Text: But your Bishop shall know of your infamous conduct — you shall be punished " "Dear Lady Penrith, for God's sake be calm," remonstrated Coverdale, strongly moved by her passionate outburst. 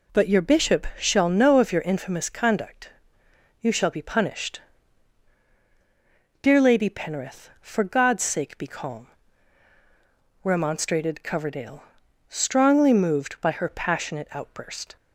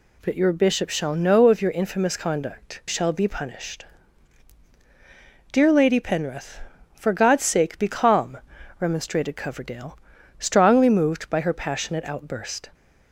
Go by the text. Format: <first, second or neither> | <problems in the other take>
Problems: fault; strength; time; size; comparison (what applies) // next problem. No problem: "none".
first | skips "you"; at 2.8 s